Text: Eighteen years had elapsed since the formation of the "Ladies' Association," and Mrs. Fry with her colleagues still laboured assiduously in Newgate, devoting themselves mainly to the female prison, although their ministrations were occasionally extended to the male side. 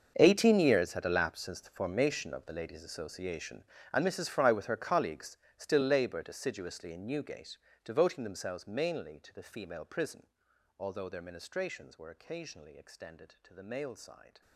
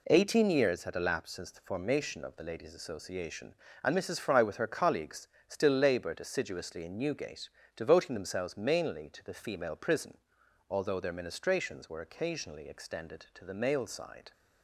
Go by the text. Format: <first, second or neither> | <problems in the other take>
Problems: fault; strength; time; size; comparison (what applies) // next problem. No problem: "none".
second | gets quieter; strong; throughout; 16.5 dB // pauses between "colleagues" and "still"; slight; at 5.3 s; 0.18 s long; slight in the second